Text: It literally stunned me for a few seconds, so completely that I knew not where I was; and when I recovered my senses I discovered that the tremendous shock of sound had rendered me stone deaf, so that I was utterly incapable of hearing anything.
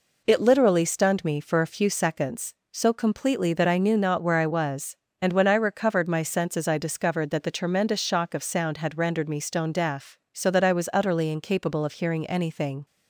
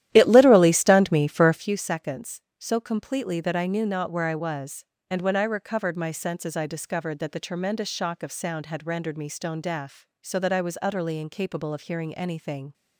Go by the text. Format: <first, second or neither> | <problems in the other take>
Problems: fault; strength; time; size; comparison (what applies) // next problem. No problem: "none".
first | starts louder than the rest; strong; until 1.7 s; 12.5 dB